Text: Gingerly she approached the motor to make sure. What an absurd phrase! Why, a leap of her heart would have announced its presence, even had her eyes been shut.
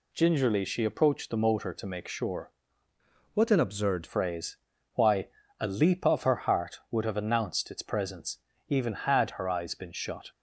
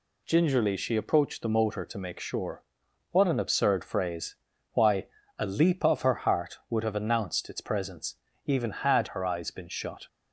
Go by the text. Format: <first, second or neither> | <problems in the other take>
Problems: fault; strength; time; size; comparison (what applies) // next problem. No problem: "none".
second | changes voice from "What" to "absurd"; from 3.3 to 4.0 s; 0.7 s long